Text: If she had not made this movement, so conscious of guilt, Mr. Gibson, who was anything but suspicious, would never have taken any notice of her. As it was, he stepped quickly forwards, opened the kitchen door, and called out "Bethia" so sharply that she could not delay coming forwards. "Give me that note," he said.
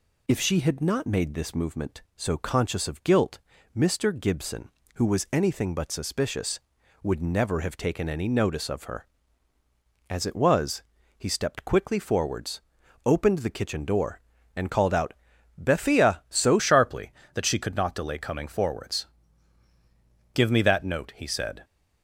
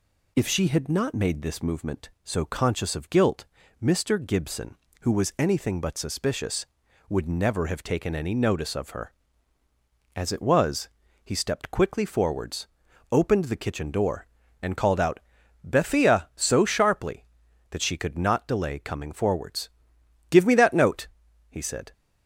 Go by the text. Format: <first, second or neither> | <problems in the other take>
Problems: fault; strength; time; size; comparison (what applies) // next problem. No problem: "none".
second | pauses between "out" and "Bethia"; at 15.1 s; 0.42 s long; also in the second // changes voice at "sharply"; from 16.5 s on; 5.1 s long